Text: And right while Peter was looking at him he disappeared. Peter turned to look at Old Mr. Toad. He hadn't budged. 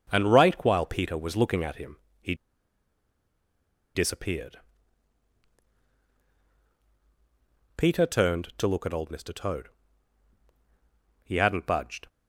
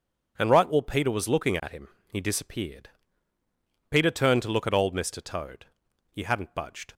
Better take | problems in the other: second | starts louder than the rest; strong; until 1.1 s; 7 dB // pauses between "him" and "he"; slight; at 1.9 s; 0.24 s long; slight in the second // pauses between "he" and "disappeared"; strong; at 2.3 s; 1.6 s long

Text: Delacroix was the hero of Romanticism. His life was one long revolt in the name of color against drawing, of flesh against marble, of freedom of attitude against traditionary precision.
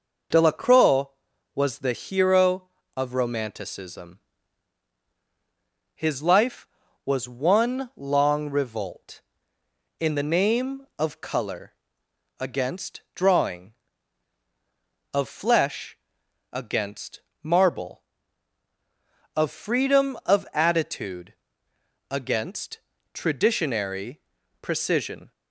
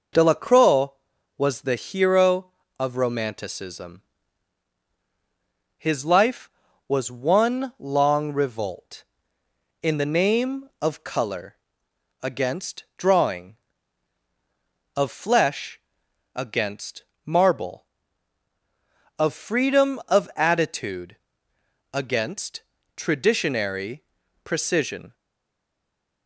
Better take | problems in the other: first | pauses between "color" and "against"; noticeable; at 11.5 s; 0.66 s long; noticeable in the first // pauses between "flesh" and "against"; noticeable; at 15.8 s; 0.56 s long; noticeable in the first // pauses between "against" and "marble"; slight; at 17.0 s; 0.24 s long; slight in the first // pauses between "attitude" and "against"; noticeable; at 21.1 s; 0.76 s long; noticeable in the first // pauses between "against" and "traditionary"; slight; at 22.6 s; 0.32 s long; slight in the first // pauses between "traditionary" and "precision"; at 24.0 s; 0.40 s long; also in the first // stays silent after the last word; from 25.1 s on; 1.1 s long

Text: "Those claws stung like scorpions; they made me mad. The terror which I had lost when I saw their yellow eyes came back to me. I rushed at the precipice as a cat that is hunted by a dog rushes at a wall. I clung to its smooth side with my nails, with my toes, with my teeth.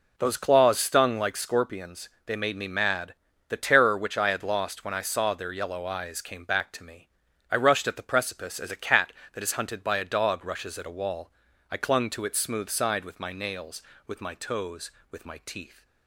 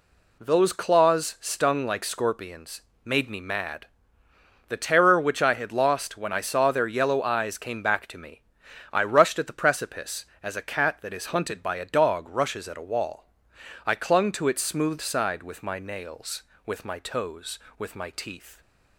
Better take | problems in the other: first | skips "they"; at 2.9 s

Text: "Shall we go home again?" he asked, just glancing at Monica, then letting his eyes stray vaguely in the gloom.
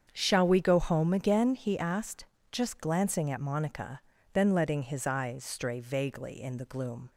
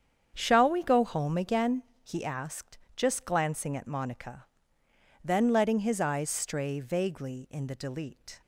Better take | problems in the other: first | starts louder than the rest; strong; until 1.3 s; 8 dB; strong in the first // says "delete" for "gloom"; at 7.7 s

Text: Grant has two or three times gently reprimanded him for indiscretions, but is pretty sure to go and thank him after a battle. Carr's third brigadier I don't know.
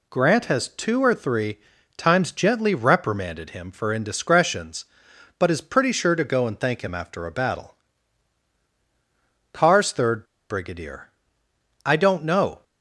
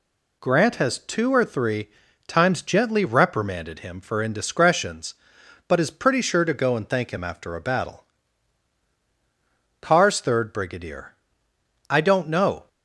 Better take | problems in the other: second | pauses between "three" and "times"; slight; at 1.5 s; 0.36 s long; slight in the second // pauses between "third" and "brigadier"; slight; at 10.2 s; 0.26 s long // pauses between "brigadier" and "I"; noticeable; at 11.0 s; 0.76 s long; noticeable in the second

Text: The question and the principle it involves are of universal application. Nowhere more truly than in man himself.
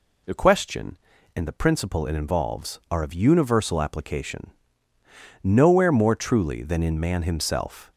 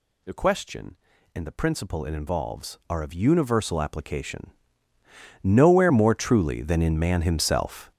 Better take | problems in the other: first | gets louder; strong; throughout; 11.5 dB

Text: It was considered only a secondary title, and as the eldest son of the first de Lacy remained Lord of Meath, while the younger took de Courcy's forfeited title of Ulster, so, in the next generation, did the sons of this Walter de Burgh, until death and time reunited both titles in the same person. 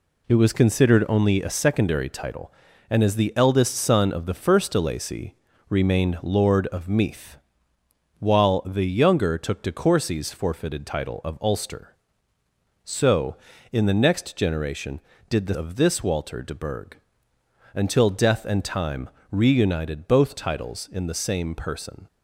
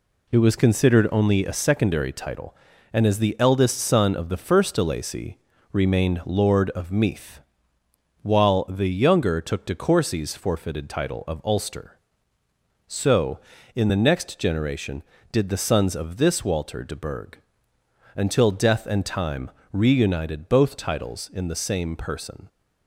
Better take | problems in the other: second | pauses between "Lacy" and "remained"; slight; at 5.3 s; 0.34 s long; slight in the second // skips "sons"; at 15.5 s // pauses between "time" and "reunited"; slight; at 19.0 s; 0.22 s long; slight in the second

